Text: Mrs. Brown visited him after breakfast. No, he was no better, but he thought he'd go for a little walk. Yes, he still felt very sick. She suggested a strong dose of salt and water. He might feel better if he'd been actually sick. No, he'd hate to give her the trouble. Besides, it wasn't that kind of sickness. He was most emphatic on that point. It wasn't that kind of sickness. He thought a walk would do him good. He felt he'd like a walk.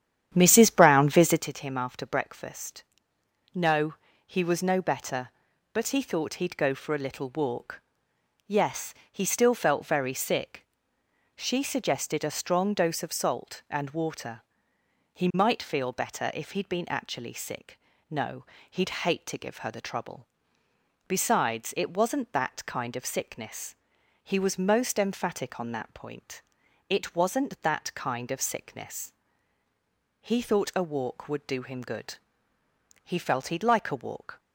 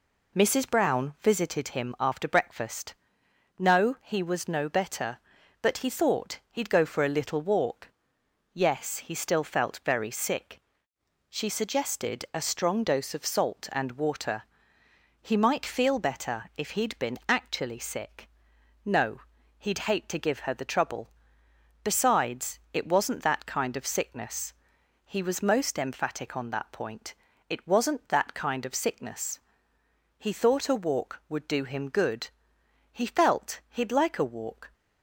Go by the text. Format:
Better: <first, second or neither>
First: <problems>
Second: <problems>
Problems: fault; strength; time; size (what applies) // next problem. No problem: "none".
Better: second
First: starts louder than the rest; strong; until 1.5 s; 10 dB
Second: none